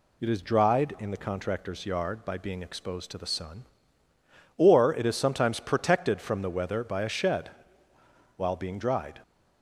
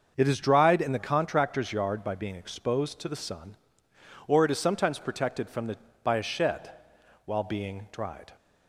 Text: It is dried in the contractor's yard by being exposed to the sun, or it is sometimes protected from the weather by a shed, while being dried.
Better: first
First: none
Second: starts louder than the rest; until 1.1 s; 6.5 dB // skips "weather"; at 5.8 s

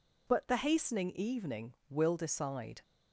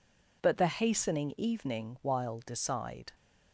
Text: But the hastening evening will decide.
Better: first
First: none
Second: says "while" for "will"; at 2.0 s

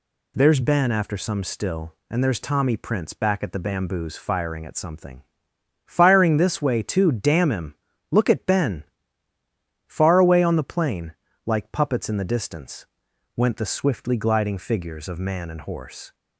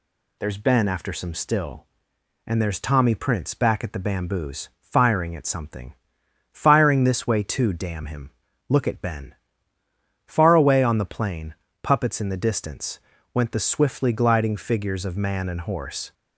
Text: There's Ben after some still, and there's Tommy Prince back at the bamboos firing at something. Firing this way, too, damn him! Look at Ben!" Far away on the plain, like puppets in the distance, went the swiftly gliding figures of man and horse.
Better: first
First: none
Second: skips "like"; at 11.6 s

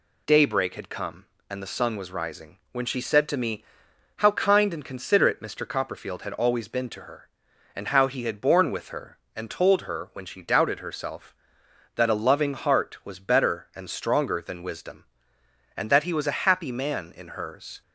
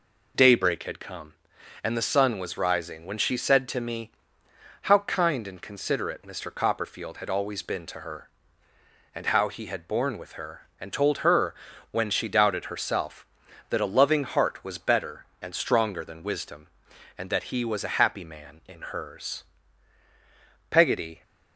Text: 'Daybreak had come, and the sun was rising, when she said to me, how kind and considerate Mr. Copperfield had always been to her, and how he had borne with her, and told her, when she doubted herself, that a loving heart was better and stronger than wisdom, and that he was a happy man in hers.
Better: first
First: none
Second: goes on to say "Peggotty"; from 20.6 s on; 0.52 s long

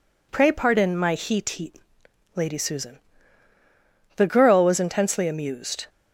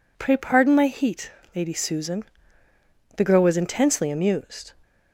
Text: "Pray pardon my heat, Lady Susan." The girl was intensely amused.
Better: second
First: says "heat" twice; at 1.4 s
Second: none

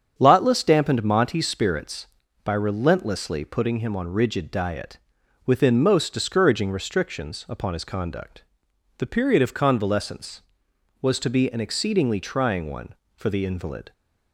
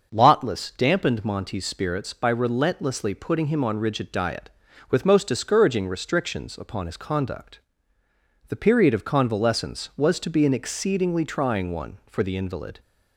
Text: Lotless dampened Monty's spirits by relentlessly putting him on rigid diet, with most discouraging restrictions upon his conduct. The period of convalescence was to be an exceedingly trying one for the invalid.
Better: second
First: starts louder than the rest; strong; until 1.1 s; 8 dB // says "within" for "with"; at 5.4 s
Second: starts louder than the rest; until 1.1 s; 6.5 dB

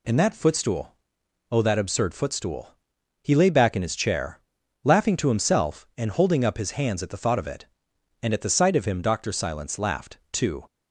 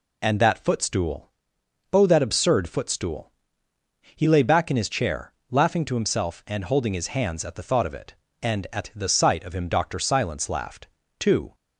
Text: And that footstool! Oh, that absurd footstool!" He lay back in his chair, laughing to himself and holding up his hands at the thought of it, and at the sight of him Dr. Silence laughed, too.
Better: first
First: none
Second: skips "up"; at 6.9 s

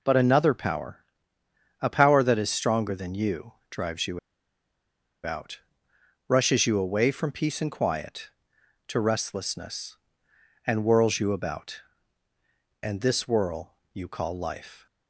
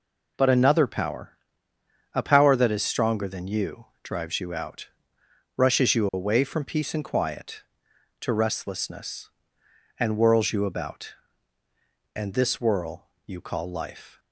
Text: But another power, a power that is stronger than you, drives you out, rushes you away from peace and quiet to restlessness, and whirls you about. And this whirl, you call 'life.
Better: second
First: pauses between "you" and "out"; at 4.1 s; 1.0 s long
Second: none

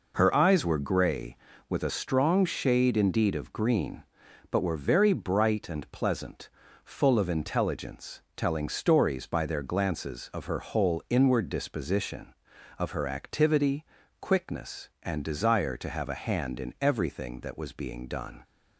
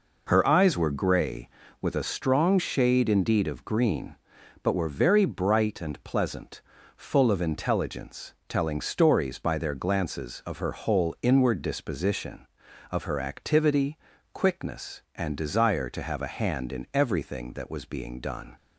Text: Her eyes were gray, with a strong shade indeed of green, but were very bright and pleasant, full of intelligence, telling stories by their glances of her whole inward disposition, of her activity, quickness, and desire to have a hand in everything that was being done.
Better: neither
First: none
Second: none

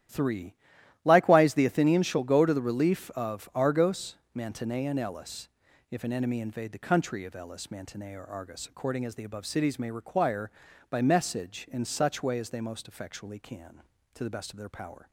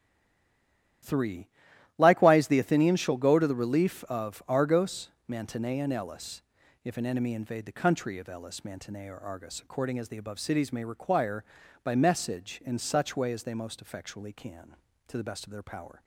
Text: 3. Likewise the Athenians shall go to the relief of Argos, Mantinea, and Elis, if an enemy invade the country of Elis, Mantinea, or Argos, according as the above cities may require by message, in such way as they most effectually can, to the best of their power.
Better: first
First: starts louder than the rest; strong; until 1.5 s; 11.5 dB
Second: stays silent before the first word; until 1.0 s; 1.0 s long // starts louder than the rest; strong; until 2.5 s; 12 dB

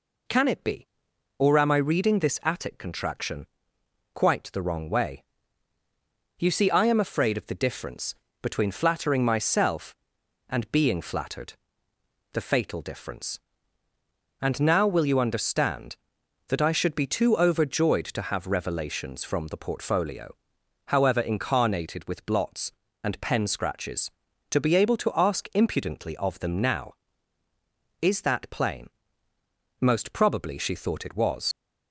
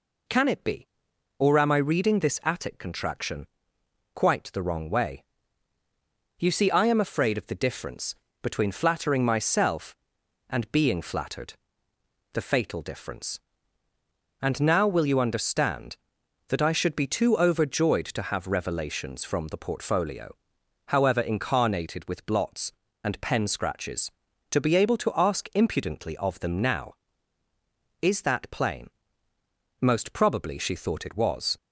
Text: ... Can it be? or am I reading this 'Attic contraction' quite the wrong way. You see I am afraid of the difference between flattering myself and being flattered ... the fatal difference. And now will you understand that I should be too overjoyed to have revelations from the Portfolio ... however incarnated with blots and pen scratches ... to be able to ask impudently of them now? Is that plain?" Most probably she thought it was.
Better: second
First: pauses between "contraction" and "quite"; noticeable; at 3.4 s; 0.70 s long // pauses between "difference" and "between"; slight; at 8.1 s; 0.26 s long // leaves "was" unfinished; at 31.5 s; 50 ms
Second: pauses between "contraction" and "quite"; noticeable; at 3.4 s; 0.70 s long // pauses between "difference" and "between"; slight; at 8.1 s; 0.26 s long

